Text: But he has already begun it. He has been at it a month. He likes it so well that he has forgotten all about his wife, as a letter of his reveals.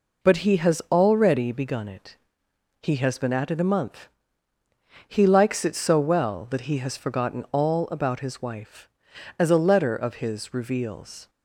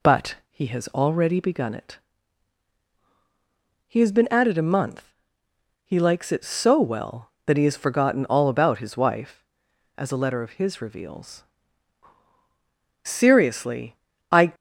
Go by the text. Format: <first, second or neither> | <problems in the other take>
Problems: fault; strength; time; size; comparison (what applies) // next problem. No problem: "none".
first | goes on to say "Seriously I"; from 13.0 s on; 1.4 s long